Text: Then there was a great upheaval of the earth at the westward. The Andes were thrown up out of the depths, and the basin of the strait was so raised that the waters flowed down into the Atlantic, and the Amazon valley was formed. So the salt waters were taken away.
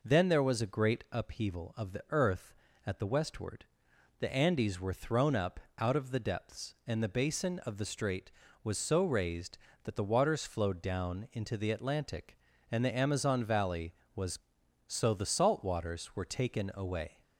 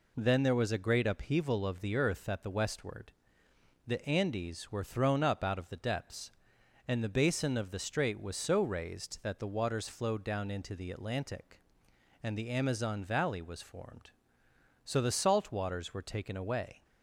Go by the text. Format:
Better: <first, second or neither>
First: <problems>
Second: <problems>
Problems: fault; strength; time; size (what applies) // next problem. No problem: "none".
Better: second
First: pauses between "up" and "out"; slight; at 5.5 s; 0.18 s long // skips "formed"; at 14.6 s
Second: none